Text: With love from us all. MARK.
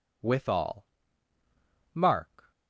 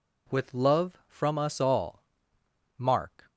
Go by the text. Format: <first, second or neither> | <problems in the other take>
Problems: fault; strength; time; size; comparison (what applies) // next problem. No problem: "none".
second | skips "love from us"; at 0.4 s